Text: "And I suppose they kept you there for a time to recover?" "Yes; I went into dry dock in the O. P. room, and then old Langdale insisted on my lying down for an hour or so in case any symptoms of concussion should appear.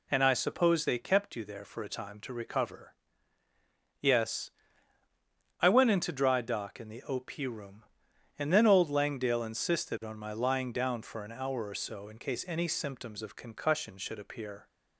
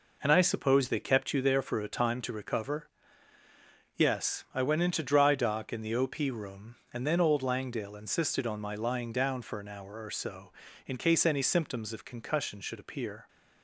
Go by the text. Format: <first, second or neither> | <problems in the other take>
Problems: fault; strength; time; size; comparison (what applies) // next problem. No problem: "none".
neither | none